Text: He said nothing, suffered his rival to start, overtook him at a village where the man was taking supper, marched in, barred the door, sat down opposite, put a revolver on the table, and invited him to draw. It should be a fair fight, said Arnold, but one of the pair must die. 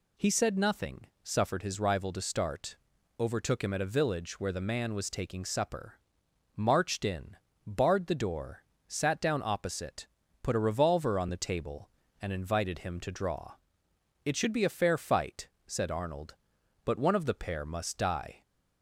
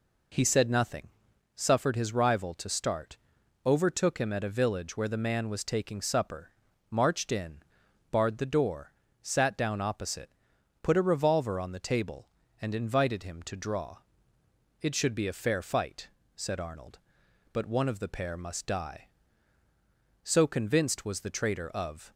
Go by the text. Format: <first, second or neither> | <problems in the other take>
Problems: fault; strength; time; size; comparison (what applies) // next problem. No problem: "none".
first | goes on to say "So convinced was the traitor of"; strong; from 20.2 s on; 1.9 s long